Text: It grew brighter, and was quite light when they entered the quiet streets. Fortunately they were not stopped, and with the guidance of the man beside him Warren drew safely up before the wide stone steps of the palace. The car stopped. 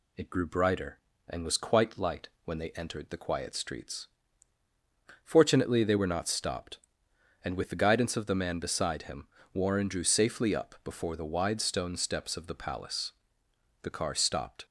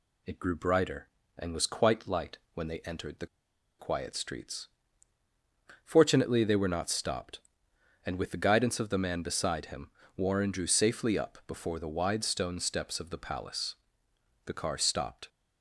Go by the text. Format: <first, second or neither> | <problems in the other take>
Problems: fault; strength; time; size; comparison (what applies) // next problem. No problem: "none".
first | pauses between "light" and "when"; slight; at 2.3 s; 0.16 s long; slight in the first // pauses between "the" and "quiet"; noticeable; at 3.2 s; 0.53 s long // pauses between "him" and "Warren"; slight; at 9.9 s; 0.26 s long; slight in the first